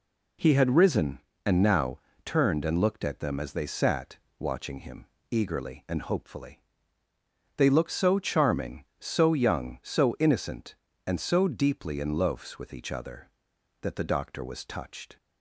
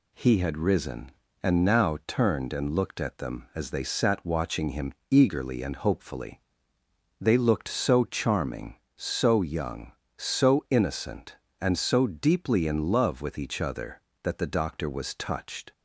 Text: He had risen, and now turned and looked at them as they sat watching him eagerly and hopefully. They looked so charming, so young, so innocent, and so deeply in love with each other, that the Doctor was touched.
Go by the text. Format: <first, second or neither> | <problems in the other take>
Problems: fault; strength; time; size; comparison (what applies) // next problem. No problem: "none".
second | pauses between "now" and "turned"; slight; at 1.9 s; 0.26 s long // pauses between "sat" and "watching"; slight; at 4.1 s; 0.20 s long // pauses between "him" and "eagerly"; slight; at 5.0 s; 0.28 s long; slight in the second // says "loafs" for "love"; at 12.1 s